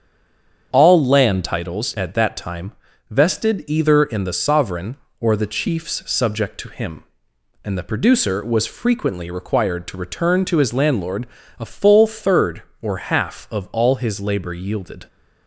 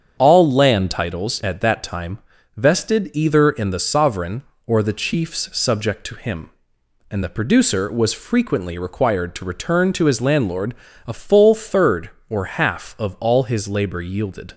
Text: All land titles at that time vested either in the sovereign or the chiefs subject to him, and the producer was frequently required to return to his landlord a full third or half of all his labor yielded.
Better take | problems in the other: second | stays silent before the first word; slight; until 0.7 s; 0.7 s long // starts louder than the rest; strong; until 1.7 s; 7.5 dB; strong in the second // pauses between "time" and "vested"; at 2.7 s; 0.38 s long; also in the second // pauses between "landlord" and "a"; slight; at 11.2 s; 0.34 s long; slight in the second

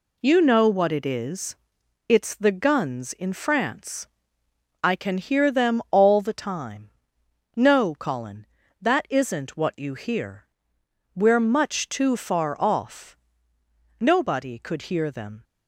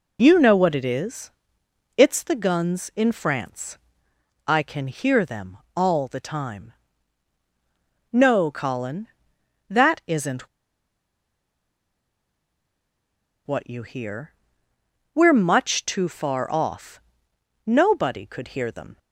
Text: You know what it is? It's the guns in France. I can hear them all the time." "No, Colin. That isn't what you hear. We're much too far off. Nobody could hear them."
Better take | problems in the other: first | pauses between "them" and "all"; slight; at 5.5 s; 0.18 s long // pauses between "isn't" and "what"; strong; at 10.4 s; 3.0 s long

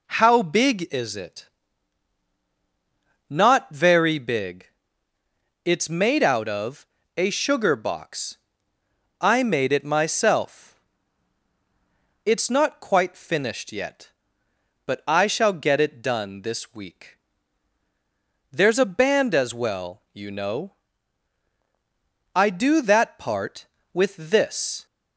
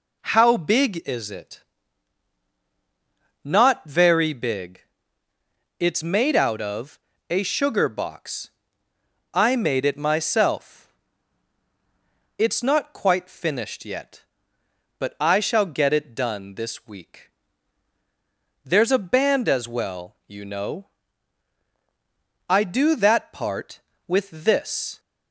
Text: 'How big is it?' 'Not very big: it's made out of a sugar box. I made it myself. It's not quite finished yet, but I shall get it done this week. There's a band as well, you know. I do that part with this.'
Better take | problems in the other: neither | pauses between "of" and "a"; slight; the same in both

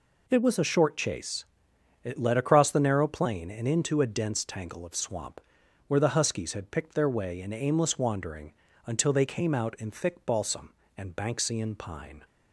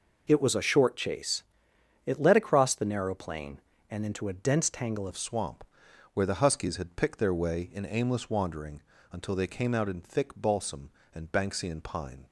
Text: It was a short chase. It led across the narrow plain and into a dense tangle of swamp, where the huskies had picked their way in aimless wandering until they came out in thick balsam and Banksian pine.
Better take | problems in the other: first | changes voice at "of"; from 5.0 s on; 7.2 s long // pauses between "wandering" and "until"; slight; at 8.8 s; 0.32 s long; slight in the first

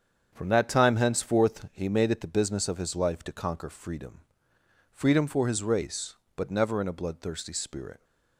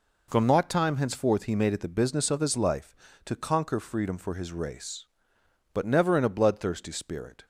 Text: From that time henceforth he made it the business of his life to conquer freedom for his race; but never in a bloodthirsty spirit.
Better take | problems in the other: second | starts louder than the rest; strong; until 1.3 s; 7.5 dB // says "freedom" twice; at 4.9 s

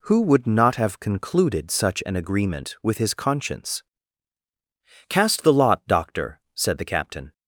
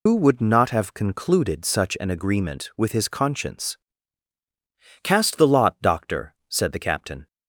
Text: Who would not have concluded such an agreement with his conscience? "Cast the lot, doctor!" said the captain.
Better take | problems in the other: first | loses the start of "Who"; at 0.0 s; 90 ms

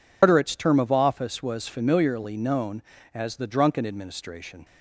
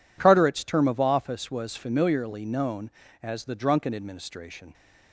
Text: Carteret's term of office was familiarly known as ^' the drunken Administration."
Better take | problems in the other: second | loses the start of "Carteret's"; at 0.2 s; 130 ms

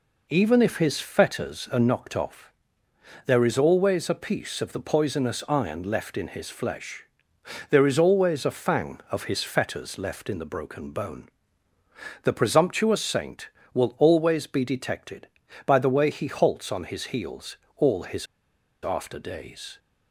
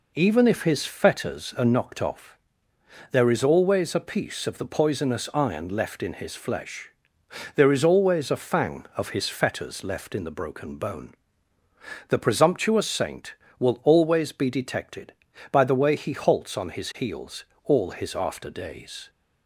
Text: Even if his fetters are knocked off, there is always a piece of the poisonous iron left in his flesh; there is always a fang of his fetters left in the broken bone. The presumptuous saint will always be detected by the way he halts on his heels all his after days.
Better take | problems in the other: second | pauses between "heels" and "all"; slight; at 17.5 s; 0.22 s long; slight in the second // pauses between "his" and "after"; noticeable; at 18.2 s; 0.58 s long

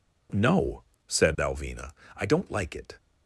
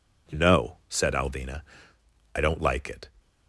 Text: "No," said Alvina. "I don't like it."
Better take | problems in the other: neither | none

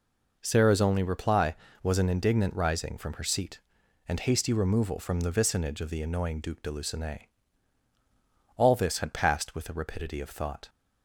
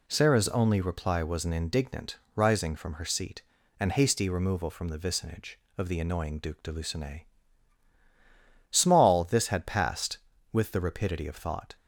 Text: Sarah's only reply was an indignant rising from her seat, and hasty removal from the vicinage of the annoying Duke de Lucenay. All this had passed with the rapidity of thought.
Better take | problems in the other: first | pauses between "indignant" and "rising"; slight; at 2.1 s; 0.20 s long // says "Small" for "All"; at 8.7 s

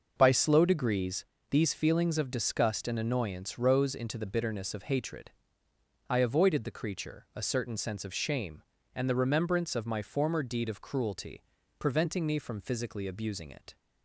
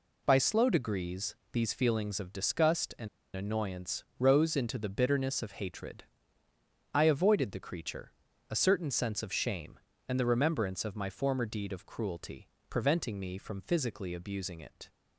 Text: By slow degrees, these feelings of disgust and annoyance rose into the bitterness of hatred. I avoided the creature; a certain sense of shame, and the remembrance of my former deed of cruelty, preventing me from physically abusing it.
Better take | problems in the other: first | pauses between "and" and "annoyance"; slight; at 3.0 s; 0.28 s long // pauses between "annoyance" and "rose"; slight; at 4.0 s; 0.16 s long

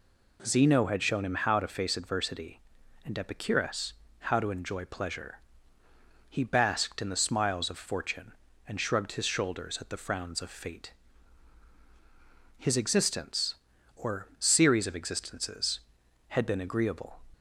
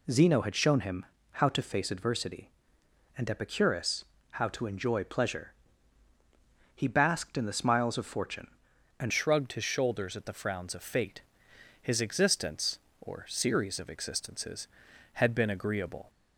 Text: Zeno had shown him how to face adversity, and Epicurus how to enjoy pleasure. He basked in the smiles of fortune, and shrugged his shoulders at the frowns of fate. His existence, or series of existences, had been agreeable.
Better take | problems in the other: first | pauses between "him" and "how"; slight; at 1.0 s; 0.28 s long // pauses between "Epicurus" and "how"; slight; at 4.0 s; 0.28 s long; slight in the first // changes voice at "shrugged"; from 9.1 s on; 6.9 s long

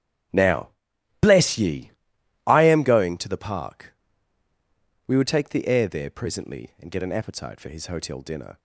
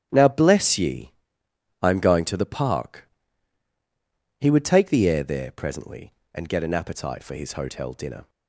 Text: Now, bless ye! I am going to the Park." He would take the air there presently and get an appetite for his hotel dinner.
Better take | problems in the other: second | starts louder than the rest; strong; until 1.8 s; 10.5 dB; strong in the second // says "We" for "He"; at 5.0 s

